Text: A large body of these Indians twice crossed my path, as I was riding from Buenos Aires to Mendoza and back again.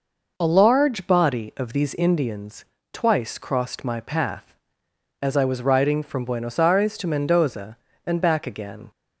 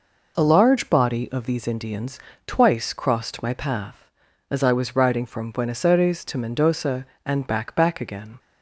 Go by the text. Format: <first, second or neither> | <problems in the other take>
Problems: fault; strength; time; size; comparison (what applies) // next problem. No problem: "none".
first | pauses between "Indians" and "twice"; slight; at 2.2 s; 0.26 s long; slight in the first // says "back" twice; at 7.7 s